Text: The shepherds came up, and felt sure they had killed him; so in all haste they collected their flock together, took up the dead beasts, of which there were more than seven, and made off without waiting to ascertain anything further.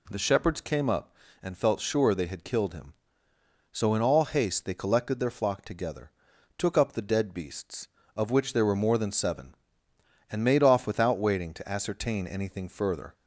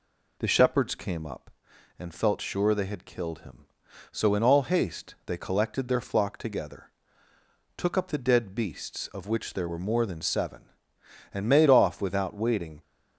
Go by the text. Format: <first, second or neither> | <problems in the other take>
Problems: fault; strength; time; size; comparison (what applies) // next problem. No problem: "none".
first | stops before "to ascertain anything further"; at 12.8 s